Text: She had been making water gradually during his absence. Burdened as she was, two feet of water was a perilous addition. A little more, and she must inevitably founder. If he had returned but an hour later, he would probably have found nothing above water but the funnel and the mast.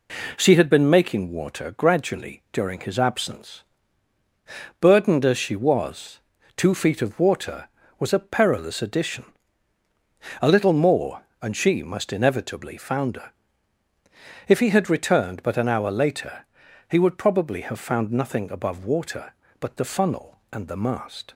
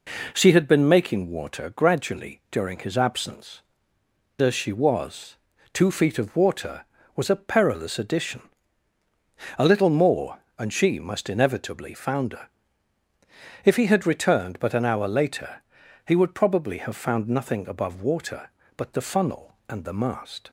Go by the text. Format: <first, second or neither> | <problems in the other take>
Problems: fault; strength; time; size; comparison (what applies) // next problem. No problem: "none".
first | skips "Burdened"; at 4.0 s